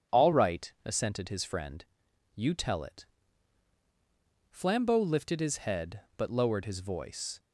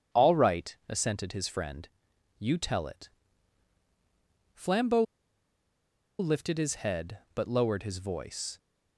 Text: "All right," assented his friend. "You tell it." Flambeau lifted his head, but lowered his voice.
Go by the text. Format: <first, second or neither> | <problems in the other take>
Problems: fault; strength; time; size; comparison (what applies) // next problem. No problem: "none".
first | starts louder than the rest; strong; until 1.2 s; 8.5 dB; strong in the first // pauses between "Flambeau" and "lifted"; at 5.0 s; 1.1 s long